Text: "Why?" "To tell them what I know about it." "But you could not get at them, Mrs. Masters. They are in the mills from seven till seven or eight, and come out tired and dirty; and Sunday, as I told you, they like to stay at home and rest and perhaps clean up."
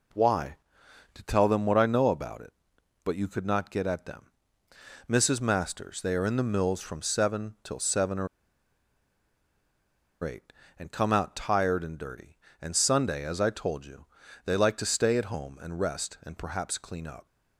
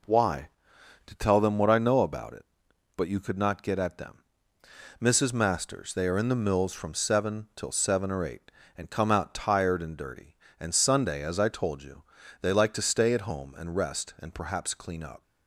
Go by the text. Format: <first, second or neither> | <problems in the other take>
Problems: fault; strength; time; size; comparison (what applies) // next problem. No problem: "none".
second | pauses between "or" and "eight"; strong; at 8.2 s; 1.9 s long